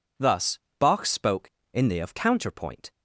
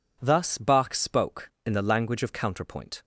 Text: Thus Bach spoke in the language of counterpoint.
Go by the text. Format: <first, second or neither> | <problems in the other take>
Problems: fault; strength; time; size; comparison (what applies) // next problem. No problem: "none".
second | pauses between "Thus" and "Bach"; slight; at 0.5 s; 0.20 s long // skips "language"; at 2.0 s